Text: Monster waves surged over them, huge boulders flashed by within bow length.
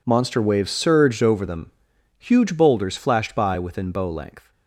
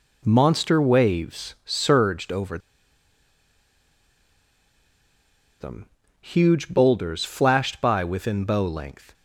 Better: first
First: none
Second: pauses between "over" and "them"; strong; at 2.5 s; 3.0 s long

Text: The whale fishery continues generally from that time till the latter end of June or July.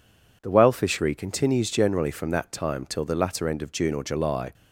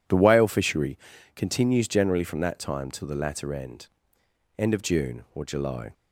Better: first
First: none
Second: pauses between "fishery" and "continues"; at 0.9 s; 0.38 s long // says "end" twice; at 4.5 s

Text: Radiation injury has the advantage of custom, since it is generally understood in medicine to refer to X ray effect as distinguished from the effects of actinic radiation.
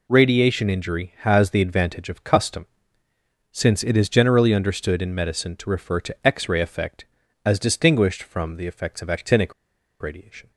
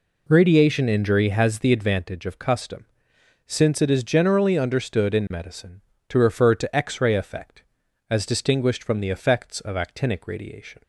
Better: second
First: pauses between "actinic" and "radiation"; noticeable; at 9.5 s; 0.49 s long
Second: none

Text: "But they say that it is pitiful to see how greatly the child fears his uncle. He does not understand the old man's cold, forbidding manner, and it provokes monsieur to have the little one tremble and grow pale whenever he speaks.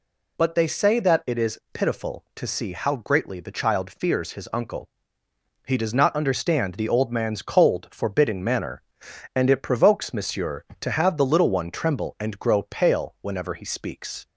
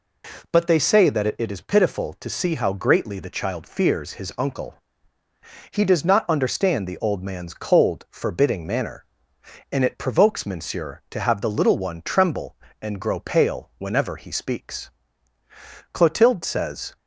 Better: first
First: none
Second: goes on to say "Clotilde says"; noticeable; from 15.9 s on; 1.0 s long

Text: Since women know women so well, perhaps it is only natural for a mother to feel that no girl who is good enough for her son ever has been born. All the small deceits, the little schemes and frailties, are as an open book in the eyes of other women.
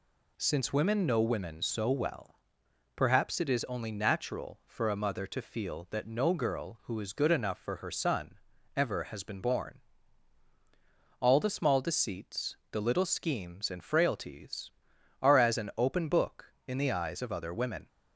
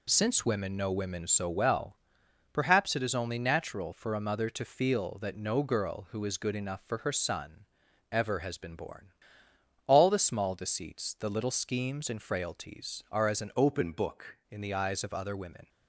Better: first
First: pauses between "son" and "ever"; at 8.3 s; 0.38 s long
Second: pauses between "son" and "ever"; at 7.6 s; 0.44 s long // changes voice from "open" to "book"; from 13.5 to 14.3 s; 0.8 s long

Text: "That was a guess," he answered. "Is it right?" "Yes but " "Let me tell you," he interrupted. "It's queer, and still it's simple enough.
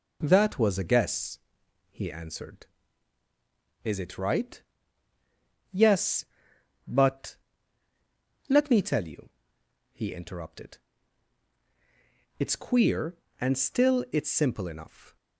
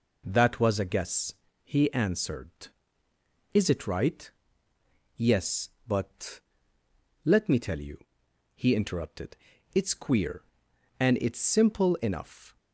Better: first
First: none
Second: skips "still"; at 11.1 s

